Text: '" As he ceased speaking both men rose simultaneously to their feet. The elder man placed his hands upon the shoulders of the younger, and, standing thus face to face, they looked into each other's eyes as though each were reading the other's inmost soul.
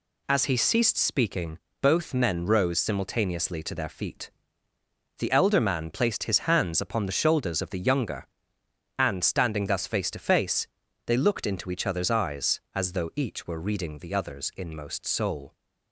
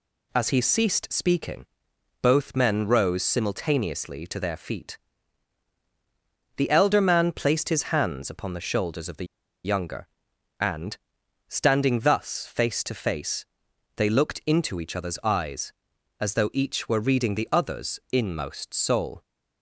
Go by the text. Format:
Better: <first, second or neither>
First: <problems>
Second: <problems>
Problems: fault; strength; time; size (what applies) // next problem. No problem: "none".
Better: first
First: pauses between "speaking" and "both"; slight; at 1.5 s; 0.24 s long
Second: pauses between "speaking" and "both"; noticeable; at 1.6 s; 0.56 s long // pauses between "the" and "younger"; at 9.2 s; 0.40 s long